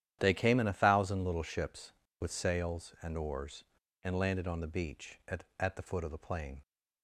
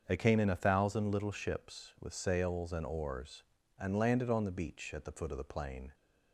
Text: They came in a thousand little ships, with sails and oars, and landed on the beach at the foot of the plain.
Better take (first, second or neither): second